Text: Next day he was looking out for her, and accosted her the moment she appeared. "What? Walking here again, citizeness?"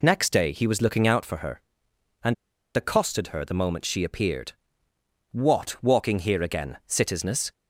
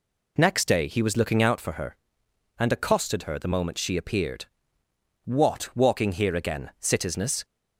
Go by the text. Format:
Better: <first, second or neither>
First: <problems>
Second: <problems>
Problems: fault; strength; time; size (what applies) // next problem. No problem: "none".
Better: second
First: pauses between "and" and "accosted"; at 2.3 s; 0.40 s long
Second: none